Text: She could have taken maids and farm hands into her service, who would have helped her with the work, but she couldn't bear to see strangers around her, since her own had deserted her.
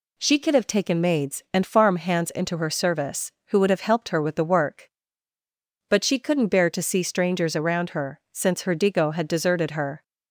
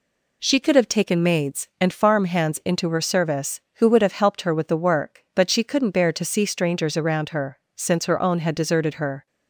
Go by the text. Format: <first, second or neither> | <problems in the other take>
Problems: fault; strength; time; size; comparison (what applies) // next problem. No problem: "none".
second | says "digo" for "own"; at 8.7 s